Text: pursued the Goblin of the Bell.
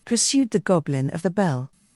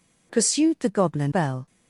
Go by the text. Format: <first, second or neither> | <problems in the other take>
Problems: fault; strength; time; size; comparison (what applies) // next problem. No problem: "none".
first | skips "of the"; at 1.3 s